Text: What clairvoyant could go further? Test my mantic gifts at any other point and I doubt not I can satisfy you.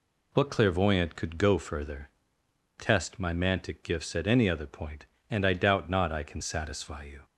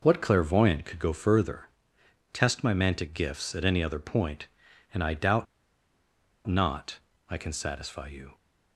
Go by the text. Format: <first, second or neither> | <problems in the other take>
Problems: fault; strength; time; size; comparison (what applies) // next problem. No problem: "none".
first | pauses between "doubt" and "not"; at 5.4 s; 1.0 s long // pauses between "not" and "I"; slight; at 6.9 s; 0.30 s long